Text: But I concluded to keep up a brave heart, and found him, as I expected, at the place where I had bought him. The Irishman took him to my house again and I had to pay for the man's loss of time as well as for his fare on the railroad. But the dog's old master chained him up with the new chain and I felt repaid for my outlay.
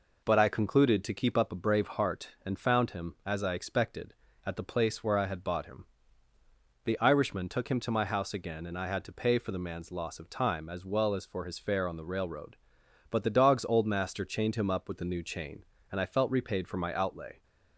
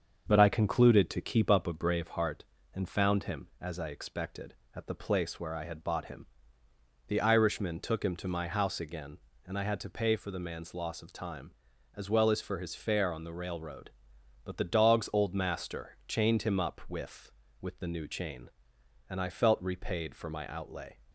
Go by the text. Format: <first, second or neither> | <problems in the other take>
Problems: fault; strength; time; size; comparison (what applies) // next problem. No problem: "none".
first | starts louder than the rest; until 1.2 s; 6.5 dB // says "with" twice; at 17.6 s